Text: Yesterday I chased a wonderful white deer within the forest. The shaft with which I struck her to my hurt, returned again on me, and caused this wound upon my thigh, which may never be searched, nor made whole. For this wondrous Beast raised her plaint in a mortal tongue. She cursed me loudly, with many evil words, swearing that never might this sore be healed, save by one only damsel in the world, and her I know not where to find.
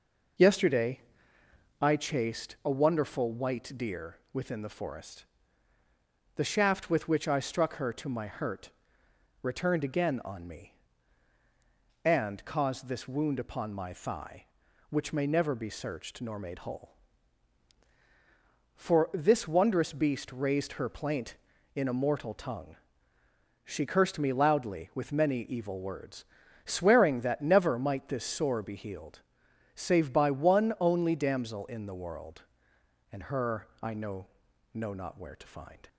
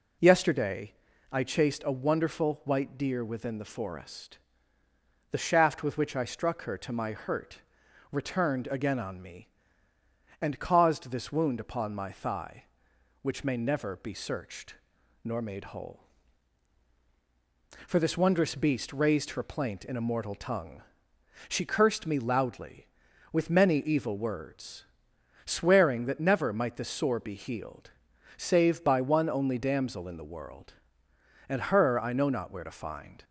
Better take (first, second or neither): second